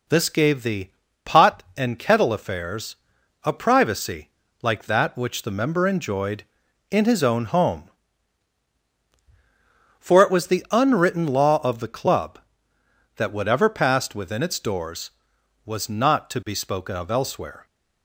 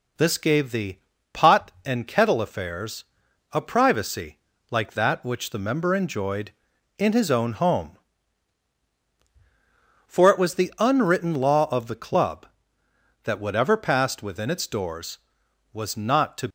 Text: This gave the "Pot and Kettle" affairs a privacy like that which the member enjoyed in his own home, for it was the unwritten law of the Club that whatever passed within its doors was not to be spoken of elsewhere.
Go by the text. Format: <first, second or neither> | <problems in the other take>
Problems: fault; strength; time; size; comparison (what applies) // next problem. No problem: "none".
first | pauses between "the" and "Pot"; slight; at 0.9 s; 0.34 s long; slight in the first // pauses between "affairs" and "a"; noticeable; at 3.0 s; 0.48 s long; noticeable in the first // pauses between "privacy" and "like"; slight; at 4.3 s; 0.32 s long; slight in the first // stops before "be spoken of elsewhere"; at 16.4 s